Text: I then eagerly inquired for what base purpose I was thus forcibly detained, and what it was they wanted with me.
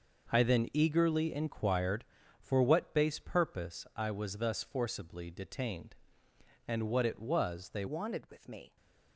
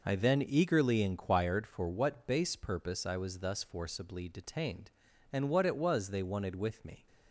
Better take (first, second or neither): second